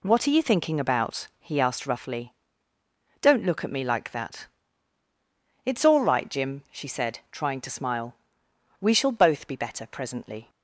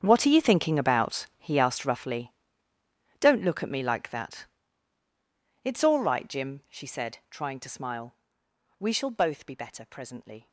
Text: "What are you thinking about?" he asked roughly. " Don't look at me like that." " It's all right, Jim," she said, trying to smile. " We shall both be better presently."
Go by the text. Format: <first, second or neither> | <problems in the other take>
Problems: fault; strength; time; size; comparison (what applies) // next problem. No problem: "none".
first | gets quieter; strong; throughout; 16 dB